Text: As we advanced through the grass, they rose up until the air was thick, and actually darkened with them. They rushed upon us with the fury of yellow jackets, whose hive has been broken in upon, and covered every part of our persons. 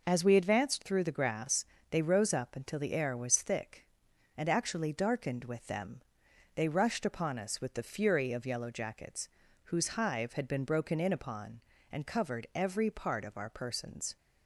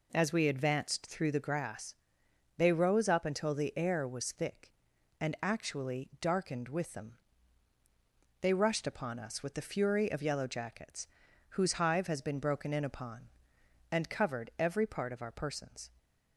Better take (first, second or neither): second